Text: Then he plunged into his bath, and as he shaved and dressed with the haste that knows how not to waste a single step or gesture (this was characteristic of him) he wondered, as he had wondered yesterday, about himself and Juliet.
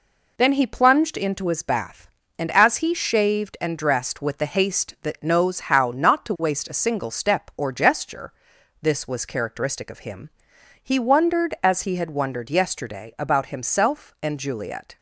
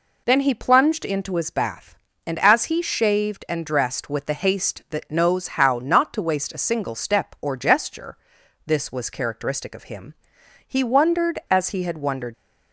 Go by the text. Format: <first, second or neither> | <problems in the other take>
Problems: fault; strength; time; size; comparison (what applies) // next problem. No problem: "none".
first | stops before "yesterday about himself and Juliet"; at 12.3 s